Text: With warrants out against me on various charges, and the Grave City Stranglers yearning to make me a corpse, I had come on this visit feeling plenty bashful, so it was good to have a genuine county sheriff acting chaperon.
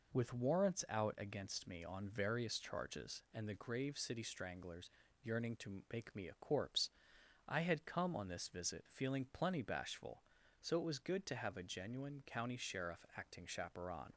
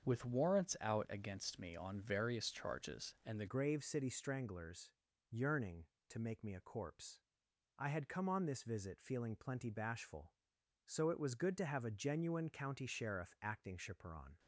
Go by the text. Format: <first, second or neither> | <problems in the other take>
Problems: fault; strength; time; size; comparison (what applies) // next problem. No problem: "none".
first | starts louder than the rest; until 1.1 s; 6.5 dB // changes voice at "Grave"; from 3.4 s on; 10.9 s long // pauses between "Stranglers" and "yearning"; at 4.9 s; 0.38 s long; slight in the first